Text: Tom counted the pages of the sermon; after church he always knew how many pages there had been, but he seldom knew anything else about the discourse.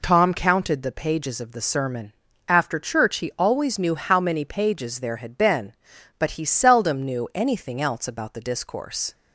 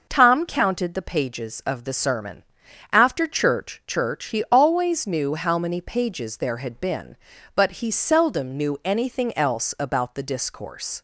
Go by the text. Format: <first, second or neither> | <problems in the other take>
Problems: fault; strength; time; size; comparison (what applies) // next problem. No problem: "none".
first | says "church" twice; at 3.8 s